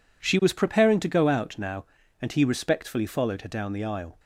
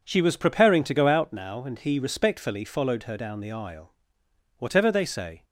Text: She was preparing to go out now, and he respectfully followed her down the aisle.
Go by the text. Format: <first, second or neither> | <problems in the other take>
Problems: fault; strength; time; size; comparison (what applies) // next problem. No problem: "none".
first | goes on to say "Whatever they say"; noticeable; from 4.5 s on; 0.86 s long